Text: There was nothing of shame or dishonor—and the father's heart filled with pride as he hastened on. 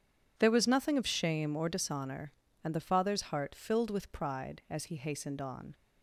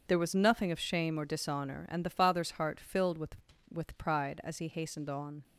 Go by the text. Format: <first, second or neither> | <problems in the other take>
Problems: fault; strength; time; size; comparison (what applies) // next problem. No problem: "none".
first | says "with" twice; at 3.6 s